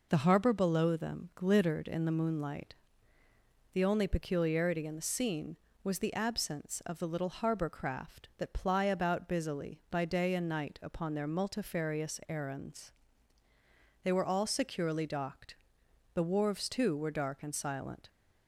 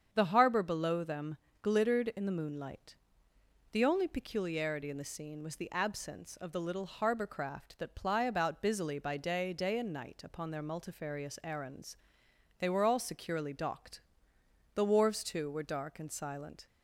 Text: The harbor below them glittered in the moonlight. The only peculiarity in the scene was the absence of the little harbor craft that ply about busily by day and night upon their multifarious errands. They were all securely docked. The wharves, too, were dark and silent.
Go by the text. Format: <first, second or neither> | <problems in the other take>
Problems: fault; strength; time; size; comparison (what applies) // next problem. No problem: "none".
first | starts louder than the rest; strong; until 1.1 s; 7.5 dB // pauses between "them" and "glittered"; slight; at 1.3 s; 0.24 s long // says "day" twice; at 9.5 s